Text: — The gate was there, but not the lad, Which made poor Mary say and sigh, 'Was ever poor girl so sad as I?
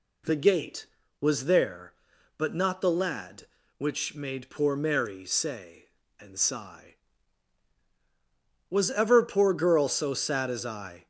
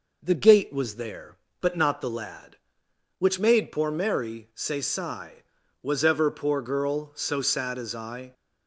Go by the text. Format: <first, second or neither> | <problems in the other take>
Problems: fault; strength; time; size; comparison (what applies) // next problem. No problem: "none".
first | skips "and"; at 4.8 s